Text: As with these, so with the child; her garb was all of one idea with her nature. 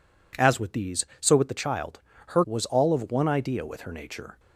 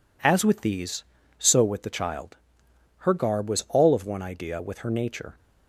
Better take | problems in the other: second | skips "garb"; at 2.4 s

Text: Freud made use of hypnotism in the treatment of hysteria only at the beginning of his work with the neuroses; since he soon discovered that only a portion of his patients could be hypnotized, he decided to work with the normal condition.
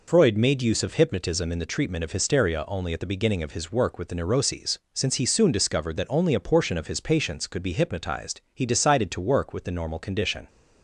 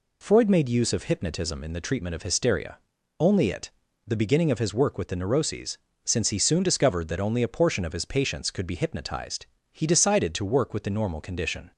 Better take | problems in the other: first | pauses between "hysteria" and "only"; at 2.7 s; 0.40 s long // says "it" for "at"; at 3.4 s

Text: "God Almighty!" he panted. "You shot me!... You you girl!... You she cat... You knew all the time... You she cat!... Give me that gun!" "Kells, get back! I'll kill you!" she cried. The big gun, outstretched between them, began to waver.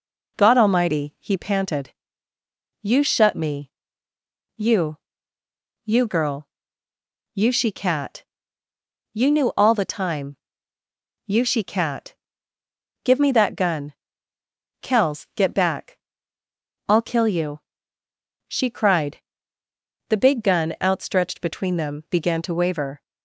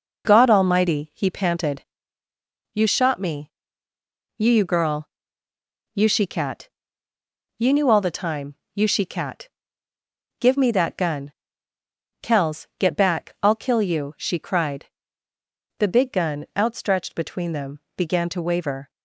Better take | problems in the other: second | says "shut" for "shot"; at 3.0 s // pauses between "You" and "you"; noticeable; at 4.9 s; 0.88 s long

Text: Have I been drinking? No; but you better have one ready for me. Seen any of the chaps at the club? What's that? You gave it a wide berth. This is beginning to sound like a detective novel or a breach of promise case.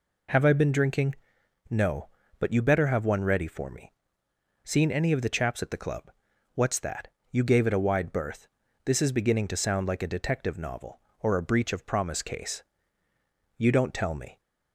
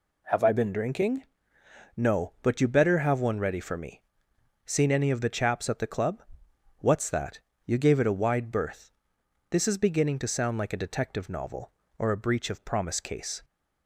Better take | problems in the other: second | goes on to say "You don't tell me"; noticeable; from 13.5 s on; 0.82 s long

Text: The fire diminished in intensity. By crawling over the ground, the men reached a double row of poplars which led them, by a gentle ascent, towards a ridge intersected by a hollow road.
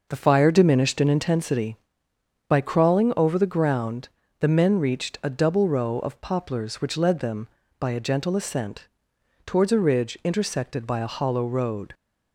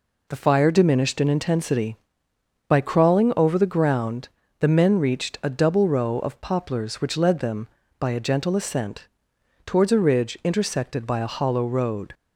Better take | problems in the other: second | starts louder than the rest; noticeable; until 1.4 s; 6 dB

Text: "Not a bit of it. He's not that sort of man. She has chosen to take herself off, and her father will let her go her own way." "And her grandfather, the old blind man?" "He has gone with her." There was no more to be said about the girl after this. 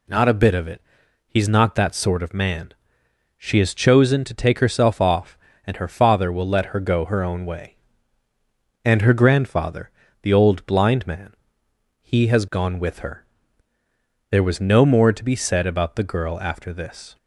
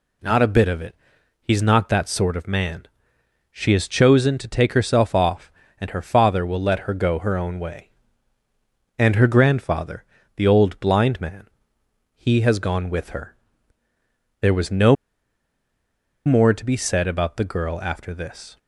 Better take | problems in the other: first | pauses between "no" and "more"; strong; at 14.9 s; 1.3 s long

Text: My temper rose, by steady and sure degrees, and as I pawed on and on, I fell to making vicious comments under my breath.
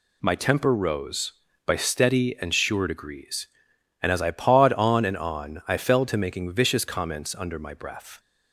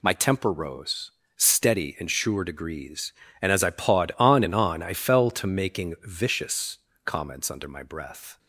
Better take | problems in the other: first | skips "by"; at 1.2 s // pauses between "vicious" and "comments"; slight; at 6.7 s; 0.26 s long

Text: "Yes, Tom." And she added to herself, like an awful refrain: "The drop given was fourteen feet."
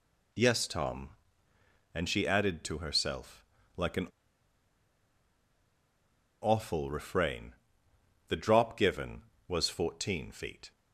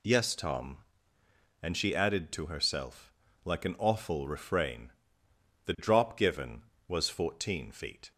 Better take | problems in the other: second | pauses between "an" and "awful"; strong; at 4.0 s; 2.3 s long

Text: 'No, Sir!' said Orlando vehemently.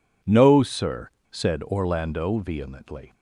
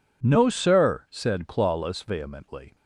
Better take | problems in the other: first | says "Clawless" for "Orlando"; at 1.4 s

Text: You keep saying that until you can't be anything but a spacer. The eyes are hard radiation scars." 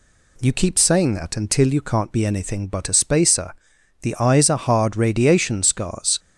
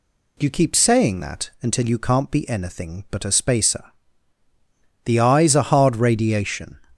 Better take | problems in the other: first | stops before "scars"; at 6.9 s

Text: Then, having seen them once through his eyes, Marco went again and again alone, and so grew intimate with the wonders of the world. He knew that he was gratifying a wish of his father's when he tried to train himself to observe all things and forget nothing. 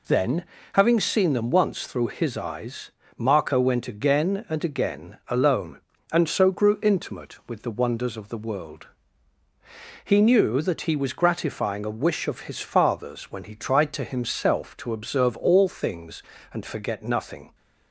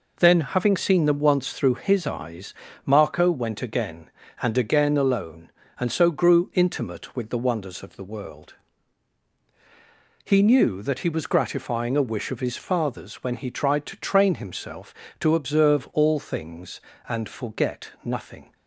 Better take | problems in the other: second | skips "train"; at 14.0 s

